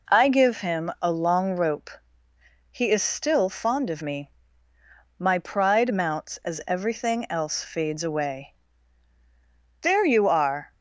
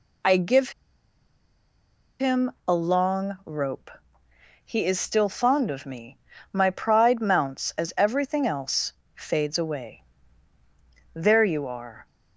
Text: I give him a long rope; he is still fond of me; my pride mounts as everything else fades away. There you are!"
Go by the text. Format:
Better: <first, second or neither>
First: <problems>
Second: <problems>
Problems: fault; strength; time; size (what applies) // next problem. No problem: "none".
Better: first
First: none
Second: pauses between "give" and "him"; strong; at 0.7 s; 1.4 s long // pauses between "him" and "a"; slight; at 2.5 s; 0.16 s long // pauses between "else" and "fades"; slight; at 8.9 s; 0.22 s long